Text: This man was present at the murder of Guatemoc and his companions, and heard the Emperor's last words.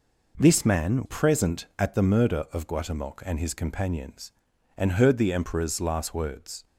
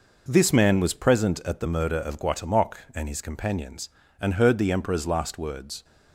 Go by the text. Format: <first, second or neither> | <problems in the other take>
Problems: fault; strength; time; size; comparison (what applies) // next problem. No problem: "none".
second | skips "was"; at 1.0 s